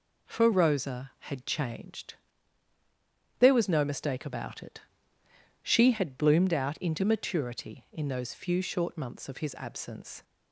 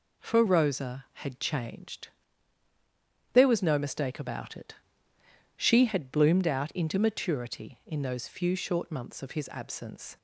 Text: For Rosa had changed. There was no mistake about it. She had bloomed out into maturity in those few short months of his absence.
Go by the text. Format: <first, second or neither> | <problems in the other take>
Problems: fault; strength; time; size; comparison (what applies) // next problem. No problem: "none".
neither | none